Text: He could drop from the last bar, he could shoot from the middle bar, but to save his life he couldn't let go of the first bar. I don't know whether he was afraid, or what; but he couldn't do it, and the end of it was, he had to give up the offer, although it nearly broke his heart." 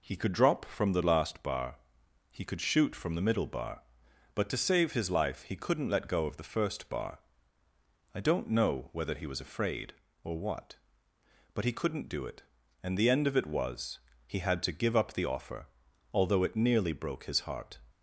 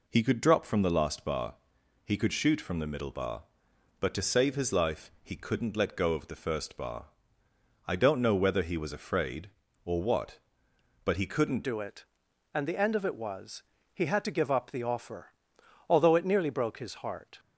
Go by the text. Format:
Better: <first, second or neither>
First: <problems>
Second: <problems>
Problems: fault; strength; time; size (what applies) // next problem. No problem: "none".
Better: first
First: none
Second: changes voice at "do"; from 11.6 s on; 5.7 s long